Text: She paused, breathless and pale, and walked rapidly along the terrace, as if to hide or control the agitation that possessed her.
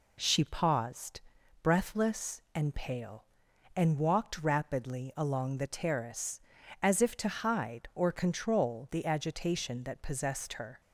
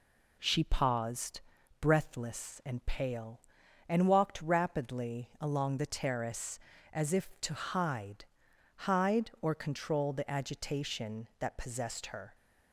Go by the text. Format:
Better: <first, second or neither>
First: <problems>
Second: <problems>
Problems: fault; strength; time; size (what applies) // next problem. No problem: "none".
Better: first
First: none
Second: says "hide" twice; at 8.8 s